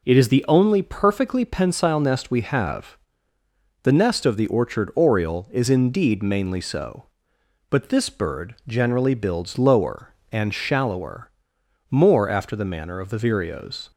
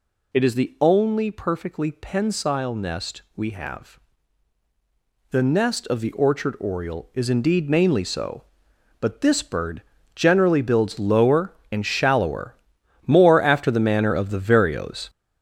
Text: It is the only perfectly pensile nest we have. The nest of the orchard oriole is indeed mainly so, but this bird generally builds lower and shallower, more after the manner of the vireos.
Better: first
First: none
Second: gets louder; strong; throughout; 7 dB // pauses between "bird" and "generally"; slight; at 9.8 s; 0.34 s long

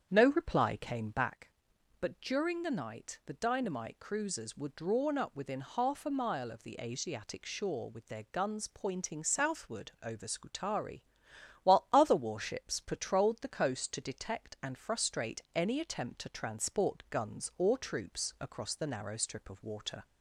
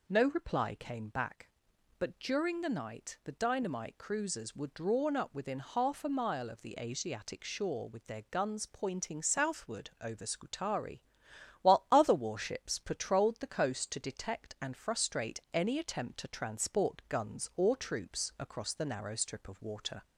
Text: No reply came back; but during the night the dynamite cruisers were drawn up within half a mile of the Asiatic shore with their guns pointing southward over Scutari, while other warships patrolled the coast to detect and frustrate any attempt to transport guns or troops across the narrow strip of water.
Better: second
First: starts louder than the rest; strong; until 1.4 s; 8 dB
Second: none

